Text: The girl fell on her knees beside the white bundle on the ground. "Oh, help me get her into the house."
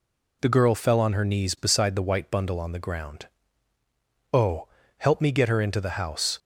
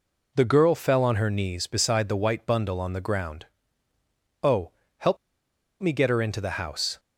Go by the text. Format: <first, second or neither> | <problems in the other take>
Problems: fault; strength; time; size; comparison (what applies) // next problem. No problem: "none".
first | pauses between "help" and "me"; noticeable; at 5.1 s; 0.64 s long